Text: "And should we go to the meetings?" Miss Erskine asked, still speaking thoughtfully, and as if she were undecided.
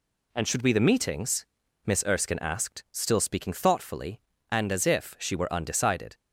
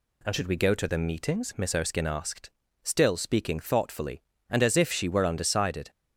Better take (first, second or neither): second